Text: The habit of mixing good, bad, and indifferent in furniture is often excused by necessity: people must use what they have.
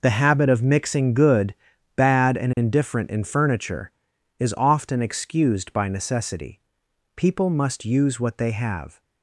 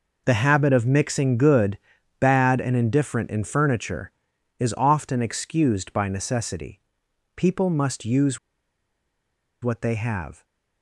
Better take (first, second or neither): first